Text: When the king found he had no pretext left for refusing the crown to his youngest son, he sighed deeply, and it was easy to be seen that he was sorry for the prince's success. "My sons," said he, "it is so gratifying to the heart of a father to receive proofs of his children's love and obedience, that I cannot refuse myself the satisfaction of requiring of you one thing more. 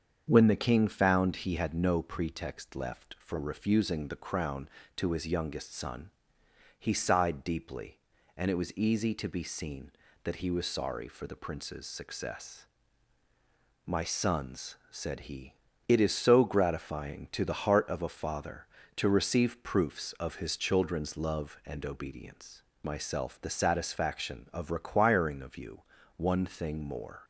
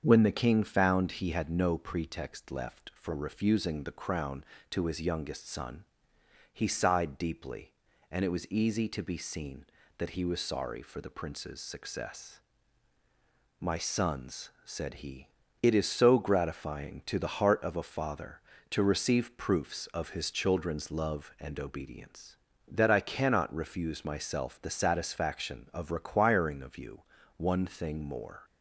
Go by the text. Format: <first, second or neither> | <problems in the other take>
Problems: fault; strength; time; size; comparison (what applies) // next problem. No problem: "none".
second | starts louder than the rest; strong; until 1.2 s; 7 dB; strong in the second // skips "that I cannot refuse"; at 22.7 s // pauses between "you" and "one"; slight; at 25.8 s; 0.34 s long; slight in the second